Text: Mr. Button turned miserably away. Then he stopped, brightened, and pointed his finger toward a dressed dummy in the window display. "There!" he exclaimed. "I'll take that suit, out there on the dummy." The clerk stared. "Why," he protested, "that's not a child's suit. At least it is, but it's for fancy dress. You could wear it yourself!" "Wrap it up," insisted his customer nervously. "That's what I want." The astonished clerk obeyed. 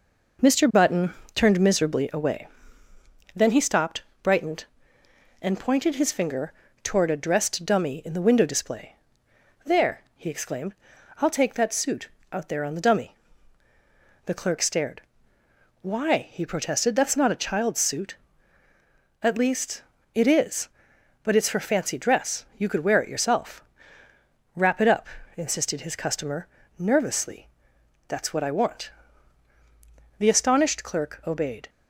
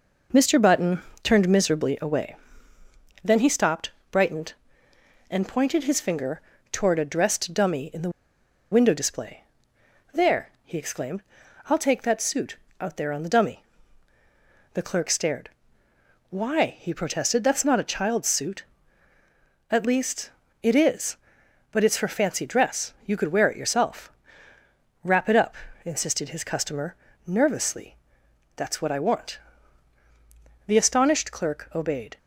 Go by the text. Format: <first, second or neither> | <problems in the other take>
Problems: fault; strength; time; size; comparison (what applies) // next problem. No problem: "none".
first | pauses between "Button" and "turned"; slight; at 1.0 s; 0.22 s long; slight in the first // pauses between "finger" and "toward"; slight; at 6.4 s; 0.30 s long; slight in the first // pauses between "the" and "window"; noticeable; at 8.0 s; 0.62 s long // pauses between "least" and "it"; slight; at 20.3 s; 0.30 s long; slight in the first // pauses between "customer" and "nervously"; slight; at 26.9 s; 0.30 s long; slight in the first